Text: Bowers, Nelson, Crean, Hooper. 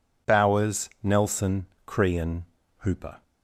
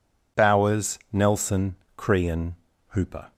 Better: neither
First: none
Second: none

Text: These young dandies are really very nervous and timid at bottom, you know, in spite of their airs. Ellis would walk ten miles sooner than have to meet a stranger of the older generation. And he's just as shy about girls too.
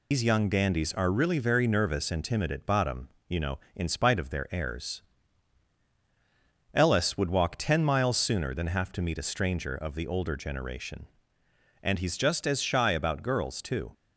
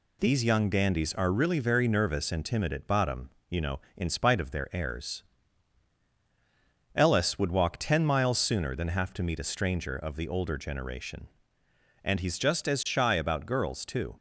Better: second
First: loses the start of "These"; at 0.1 s; 120 ms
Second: none

